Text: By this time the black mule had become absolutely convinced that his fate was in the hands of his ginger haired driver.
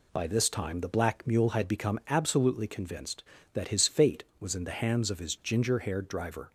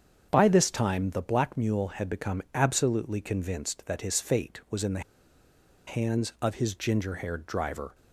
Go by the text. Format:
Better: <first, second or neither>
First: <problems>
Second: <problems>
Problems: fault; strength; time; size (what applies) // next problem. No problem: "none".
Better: first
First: none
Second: starts louder than the rest; strong; until 1.3 s; 7.5 dB // pauses between "the" and "hands"; noticeable; at 5.0 s; 0.86 s long